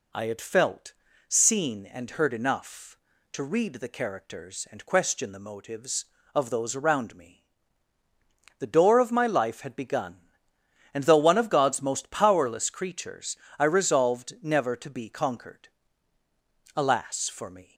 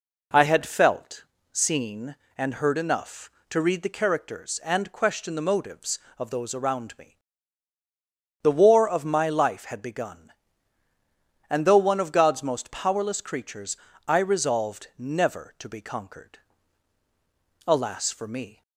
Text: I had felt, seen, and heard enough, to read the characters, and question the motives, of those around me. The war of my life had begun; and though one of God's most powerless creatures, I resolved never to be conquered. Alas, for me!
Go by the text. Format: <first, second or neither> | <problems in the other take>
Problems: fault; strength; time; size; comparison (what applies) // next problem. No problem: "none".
second | says "door" for "war"; at 8.6 s